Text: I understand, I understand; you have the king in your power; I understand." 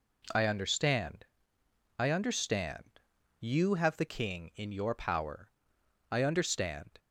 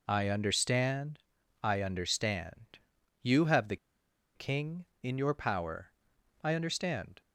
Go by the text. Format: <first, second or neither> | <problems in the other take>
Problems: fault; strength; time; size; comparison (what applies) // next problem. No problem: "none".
first | pauses between "the" and "king"; noticeable; at 3.7 s; 0.59 s long